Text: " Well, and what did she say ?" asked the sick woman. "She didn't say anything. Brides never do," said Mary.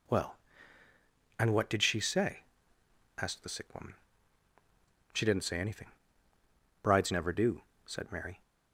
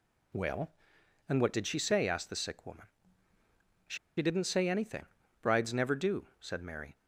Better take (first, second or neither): first